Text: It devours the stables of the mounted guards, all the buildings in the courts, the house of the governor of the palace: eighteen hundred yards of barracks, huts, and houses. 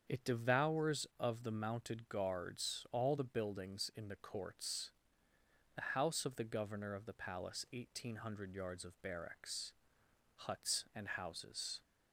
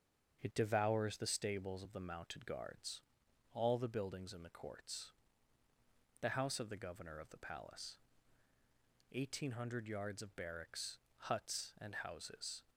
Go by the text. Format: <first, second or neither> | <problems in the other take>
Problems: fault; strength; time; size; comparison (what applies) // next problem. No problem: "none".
second | starts louder than the rest; until 1.2 s; 7 dB; also in the second // skips "the stables"; at 1.1 s